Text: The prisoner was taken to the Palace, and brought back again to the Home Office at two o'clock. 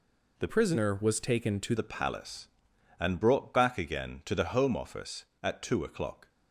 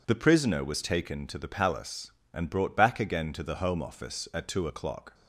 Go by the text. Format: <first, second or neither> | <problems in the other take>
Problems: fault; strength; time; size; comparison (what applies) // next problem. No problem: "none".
second | changes voice from "prisoner" to "to"; from 0.4 to 1.7 s; 1.3 s long